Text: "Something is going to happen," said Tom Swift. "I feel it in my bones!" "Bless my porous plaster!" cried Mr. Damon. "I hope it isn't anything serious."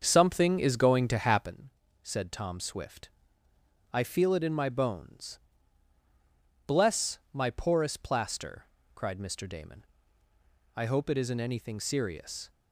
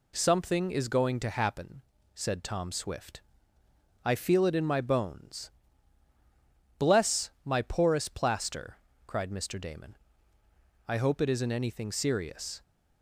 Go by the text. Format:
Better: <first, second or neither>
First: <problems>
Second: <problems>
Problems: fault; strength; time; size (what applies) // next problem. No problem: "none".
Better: second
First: starts louder than the rest; until 1.5 s; 7 dB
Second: none